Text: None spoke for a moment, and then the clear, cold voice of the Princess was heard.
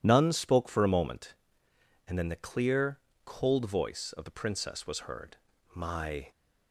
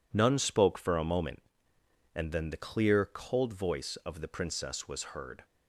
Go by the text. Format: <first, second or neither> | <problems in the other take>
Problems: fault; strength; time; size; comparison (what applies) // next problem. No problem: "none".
second | goes on to say "My"; from 5.7 s on; 0.54 s long